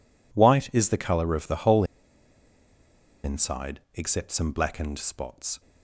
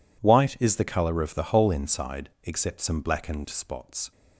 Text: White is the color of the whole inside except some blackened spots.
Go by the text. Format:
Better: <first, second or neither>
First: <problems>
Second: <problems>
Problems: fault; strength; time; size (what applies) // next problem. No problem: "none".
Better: second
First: pauses between "whole" and "inside"; strong; at 1.8 s; 1.3 s long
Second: none